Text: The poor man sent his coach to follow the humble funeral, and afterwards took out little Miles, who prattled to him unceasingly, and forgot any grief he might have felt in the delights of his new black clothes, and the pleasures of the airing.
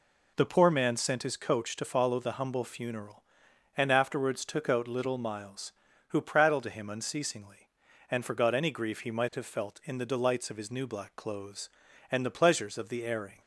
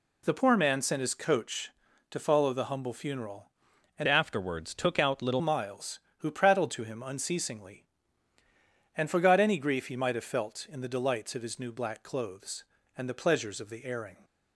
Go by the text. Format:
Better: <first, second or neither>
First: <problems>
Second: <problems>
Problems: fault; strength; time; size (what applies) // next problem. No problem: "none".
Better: first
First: none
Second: changes voice from "afterwards" to "little"; from 4.0 to 5.3 s; 1.3 s long